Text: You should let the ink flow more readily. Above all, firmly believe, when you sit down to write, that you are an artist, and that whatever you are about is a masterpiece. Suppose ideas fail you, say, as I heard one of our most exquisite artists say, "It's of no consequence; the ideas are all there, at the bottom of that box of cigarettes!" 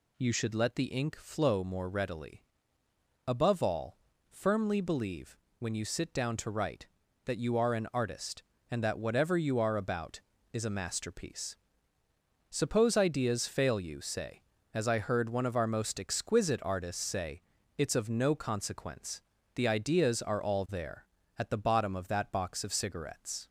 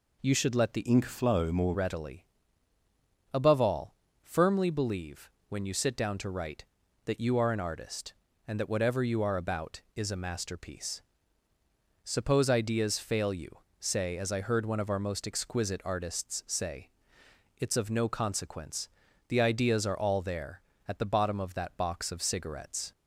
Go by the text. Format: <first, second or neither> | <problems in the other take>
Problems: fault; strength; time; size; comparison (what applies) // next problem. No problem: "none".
first | changes voice from "ink" to "more"; from 0.8 to 1.7 s; 0.9 s long